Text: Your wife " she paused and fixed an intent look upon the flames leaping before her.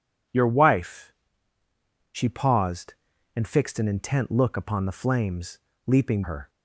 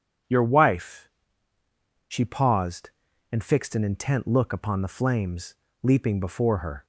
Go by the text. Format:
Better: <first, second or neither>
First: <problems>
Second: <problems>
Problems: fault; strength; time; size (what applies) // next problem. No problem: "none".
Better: second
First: starts louder than the rest; strong; until 1.8 s; 8 dB // pauses between "flames" and "leaping"; slight; at 5.5 s; 0.28 s long // skips "before"; at 6.2 s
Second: starts louder than the rest; strong; until 1.7 s; 7.5 dB // pauses between "flames" and "leaping"; slight; at 5.5 s; 0.28 s long